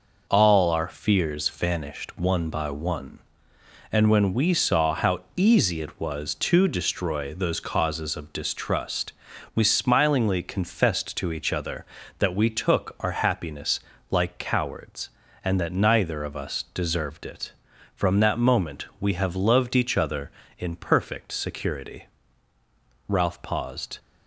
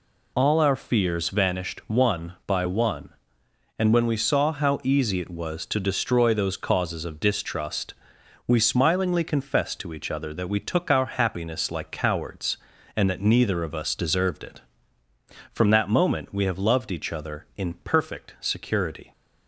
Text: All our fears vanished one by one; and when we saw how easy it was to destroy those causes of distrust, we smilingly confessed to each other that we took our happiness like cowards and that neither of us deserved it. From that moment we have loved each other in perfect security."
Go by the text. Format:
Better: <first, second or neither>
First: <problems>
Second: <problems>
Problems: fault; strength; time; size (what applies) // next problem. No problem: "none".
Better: second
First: pauses between "how" and "easy"; slight; at 5.2 s; 0.16 s long // pauses between "happiness" and "like"; slight; at 13.7 s; 0.32 s long // goes on to say "Ralph paused"; noticeable; from 23.0 s on; 0.92 s long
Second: none